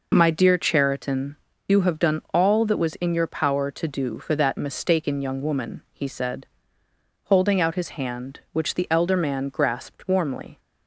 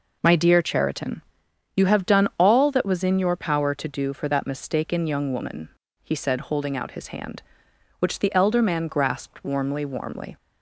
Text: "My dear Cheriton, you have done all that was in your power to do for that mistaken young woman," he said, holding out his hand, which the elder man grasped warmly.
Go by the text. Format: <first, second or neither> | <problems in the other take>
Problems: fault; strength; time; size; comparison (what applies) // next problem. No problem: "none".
first | says "warmly" twice; at 9.8 s